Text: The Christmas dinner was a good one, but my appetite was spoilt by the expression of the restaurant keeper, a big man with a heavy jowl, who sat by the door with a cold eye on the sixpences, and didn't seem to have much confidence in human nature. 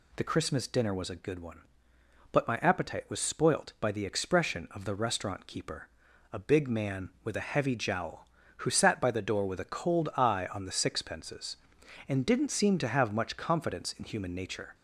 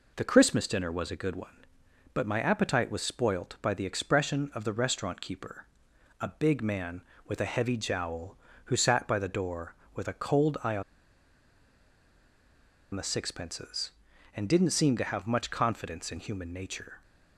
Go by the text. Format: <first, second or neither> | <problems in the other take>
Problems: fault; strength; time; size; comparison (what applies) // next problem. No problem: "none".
first | pauses between "on" and "the"; strong; at 10.8 s; 2.1 s long